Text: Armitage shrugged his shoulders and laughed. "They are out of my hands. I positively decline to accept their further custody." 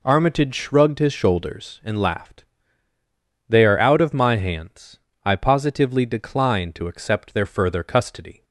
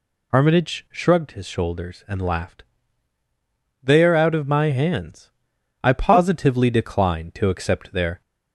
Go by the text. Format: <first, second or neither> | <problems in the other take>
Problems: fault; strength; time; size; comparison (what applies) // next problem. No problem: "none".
first | stops before "further custody"; at 8.2 s